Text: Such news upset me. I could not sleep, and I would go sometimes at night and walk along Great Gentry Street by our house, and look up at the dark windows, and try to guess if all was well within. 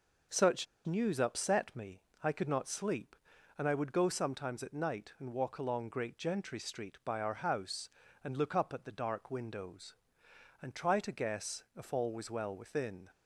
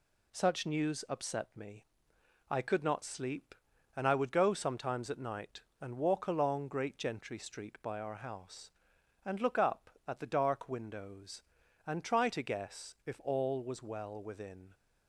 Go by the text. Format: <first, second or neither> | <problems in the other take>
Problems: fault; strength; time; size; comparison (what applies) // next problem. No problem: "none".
second | pauses between "Such" and "news"; slight; at 0.6 s; 0.21 s long